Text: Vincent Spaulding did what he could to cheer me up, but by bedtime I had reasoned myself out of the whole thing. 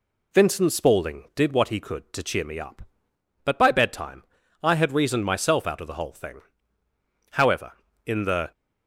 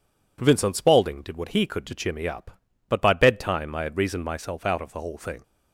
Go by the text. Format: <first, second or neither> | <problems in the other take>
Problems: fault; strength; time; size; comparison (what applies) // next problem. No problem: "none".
second | pauses between "bedtime" and "I"; at 4.2 s; 0.40 s long // goes on to say "However in the"; noticeable; from 7.3 s on; 1.2 s long